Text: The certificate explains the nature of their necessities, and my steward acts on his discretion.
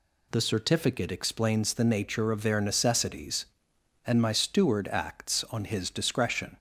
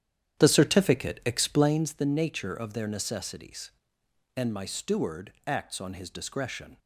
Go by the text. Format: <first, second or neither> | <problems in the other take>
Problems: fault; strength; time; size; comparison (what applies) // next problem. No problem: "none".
first | starts louder than the rest; strong; until 1.8 s; 10 dB // pauses between "steward" and "acts"; slight; at 5.3 s; 0.16 s long